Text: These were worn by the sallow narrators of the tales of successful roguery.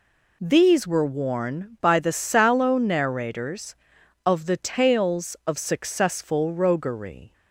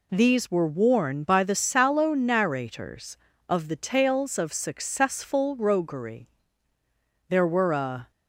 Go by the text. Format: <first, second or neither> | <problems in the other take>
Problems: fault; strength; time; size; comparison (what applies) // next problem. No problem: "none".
first | goes on to say "There were a"; noticeable; from 7.2 s on; 0.82 s long